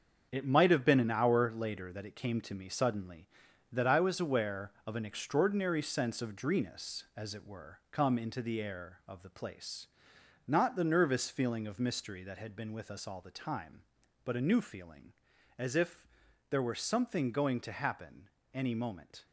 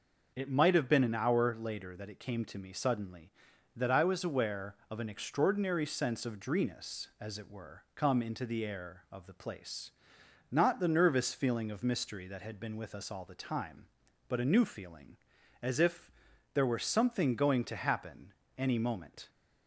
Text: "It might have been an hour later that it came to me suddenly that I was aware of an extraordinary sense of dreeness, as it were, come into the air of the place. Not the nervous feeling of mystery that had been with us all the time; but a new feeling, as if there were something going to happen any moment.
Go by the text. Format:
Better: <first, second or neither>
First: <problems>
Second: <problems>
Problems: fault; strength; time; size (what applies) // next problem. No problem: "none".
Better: second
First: gets quieter; strong; throughout; 8.5 dB // pauses between "if" and "there"; at 16.0 s; 0.42 s long // pauses between "happen" and "any"; slight; at 18.2 s; 0.22 s long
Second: pauses between "if" and "there"; at 16.1 s; 0.42 s long // pauses between "happen" and "any"; slight; at 18.3 s; 0.22 s long